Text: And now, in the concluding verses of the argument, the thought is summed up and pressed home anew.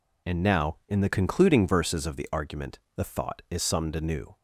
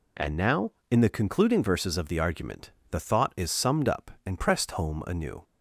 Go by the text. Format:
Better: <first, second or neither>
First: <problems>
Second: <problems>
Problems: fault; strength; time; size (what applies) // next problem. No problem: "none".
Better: second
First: skips "up and pressed home"; at 3.9 s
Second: none